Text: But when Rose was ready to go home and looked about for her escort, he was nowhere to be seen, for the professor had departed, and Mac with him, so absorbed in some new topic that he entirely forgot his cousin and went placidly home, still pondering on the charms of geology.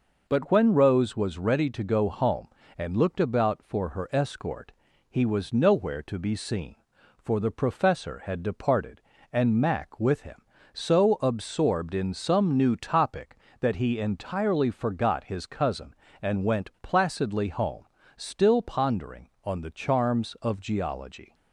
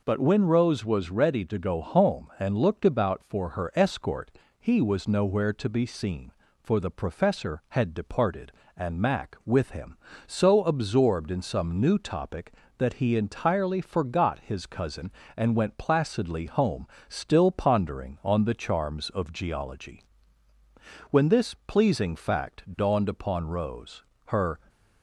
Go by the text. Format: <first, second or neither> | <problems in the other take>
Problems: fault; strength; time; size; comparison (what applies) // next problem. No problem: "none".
first | goes on to say "When this pleasing fact dawned upon Rose her"; strong; from 21.1 s on; 3.4 s long